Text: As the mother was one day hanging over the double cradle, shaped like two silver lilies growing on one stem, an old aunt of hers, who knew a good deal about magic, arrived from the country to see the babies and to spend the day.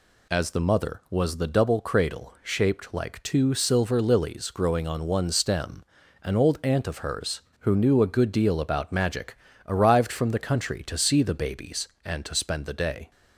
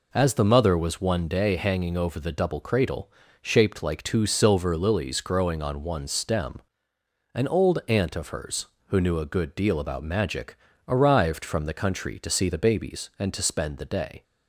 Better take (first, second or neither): second